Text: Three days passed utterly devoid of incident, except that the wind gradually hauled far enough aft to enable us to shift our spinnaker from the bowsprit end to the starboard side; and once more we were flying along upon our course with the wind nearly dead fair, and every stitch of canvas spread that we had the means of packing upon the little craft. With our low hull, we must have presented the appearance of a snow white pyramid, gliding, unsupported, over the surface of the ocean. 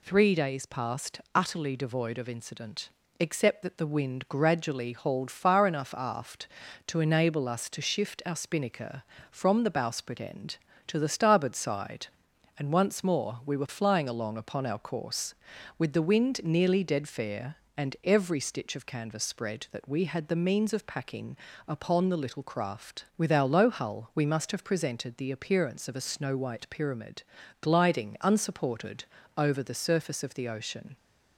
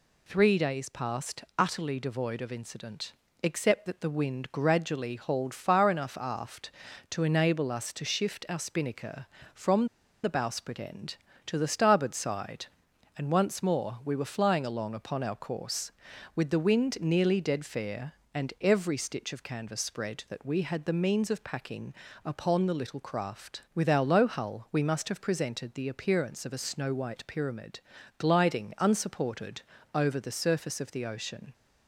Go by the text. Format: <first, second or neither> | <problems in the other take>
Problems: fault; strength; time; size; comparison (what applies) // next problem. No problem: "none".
first | pauses between "from" and "the"; at 9.8 s; 0.36 s long // pauses between "packing" and "upon"; slight; at 21.9 s; 0.32 s long; slight in the first